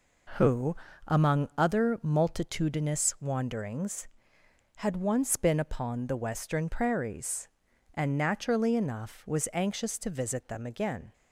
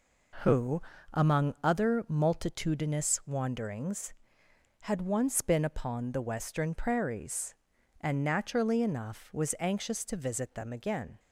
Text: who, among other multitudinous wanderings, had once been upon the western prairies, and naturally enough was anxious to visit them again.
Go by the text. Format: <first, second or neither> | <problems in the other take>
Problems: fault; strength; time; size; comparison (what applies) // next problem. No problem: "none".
neither | none